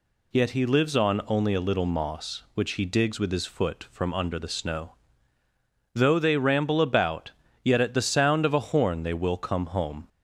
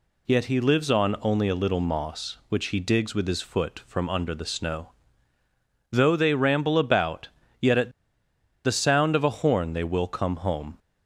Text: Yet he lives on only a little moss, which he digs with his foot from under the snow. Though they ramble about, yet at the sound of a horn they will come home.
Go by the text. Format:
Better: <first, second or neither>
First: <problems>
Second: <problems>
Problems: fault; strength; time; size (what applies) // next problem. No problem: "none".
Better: first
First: none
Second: pauses between "at" and "the"; noticeable; at 7.9 s; 0.73 s long